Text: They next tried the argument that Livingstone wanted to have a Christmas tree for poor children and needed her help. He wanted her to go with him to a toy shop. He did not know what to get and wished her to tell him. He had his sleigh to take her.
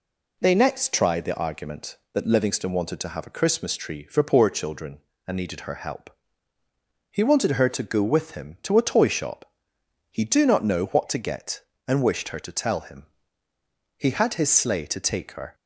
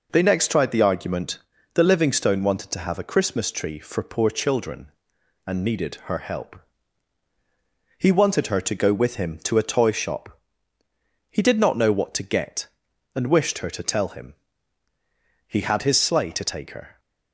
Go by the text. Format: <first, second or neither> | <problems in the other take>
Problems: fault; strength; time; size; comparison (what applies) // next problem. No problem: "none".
second | says "do" for "did"; at 10.2 s